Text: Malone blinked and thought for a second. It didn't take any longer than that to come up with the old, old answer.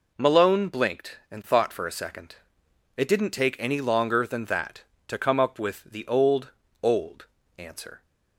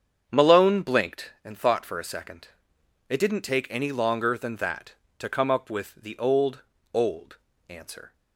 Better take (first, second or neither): first